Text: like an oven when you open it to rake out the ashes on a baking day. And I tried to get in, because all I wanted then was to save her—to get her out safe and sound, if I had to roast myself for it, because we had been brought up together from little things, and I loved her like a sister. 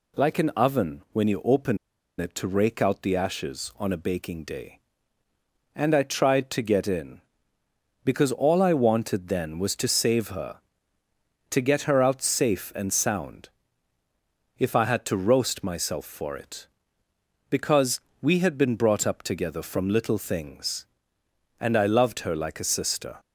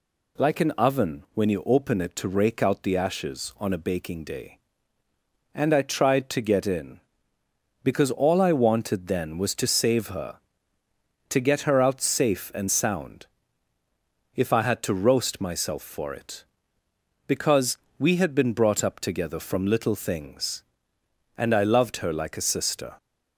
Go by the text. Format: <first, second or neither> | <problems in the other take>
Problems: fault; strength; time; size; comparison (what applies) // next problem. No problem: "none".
second | pauses between "open" and "it"; at 1.7 s; 0.43 s long // pauses between "because" and "we"; slight; at 17.9 s; 0.22 s long; slight in the second